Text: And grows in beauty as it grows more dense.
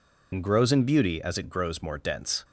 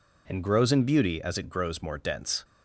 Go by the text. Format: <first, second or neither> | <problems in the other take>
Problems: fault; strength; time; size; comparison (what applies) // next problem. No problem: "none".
second | loses the start of "And"; at 0.3 s; 60 ms